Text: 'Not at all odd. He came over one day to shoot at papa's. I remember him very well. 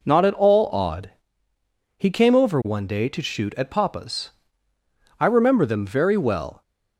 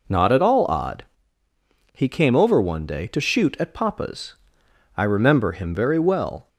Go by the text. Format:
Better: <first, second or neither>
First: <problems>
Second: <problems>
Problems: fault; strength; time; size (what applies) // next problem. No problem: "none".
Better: second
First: says "them" for "him"; at 5.6 s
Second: none